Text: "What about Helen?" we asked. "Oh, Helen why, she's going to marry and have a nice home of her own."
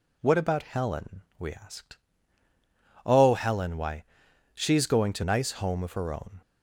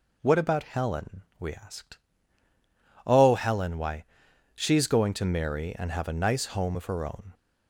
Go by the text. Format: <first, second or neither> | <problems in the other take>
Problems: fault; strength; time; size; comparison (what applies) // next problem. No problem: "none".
second | skips "marry and have a"; at 5.2 s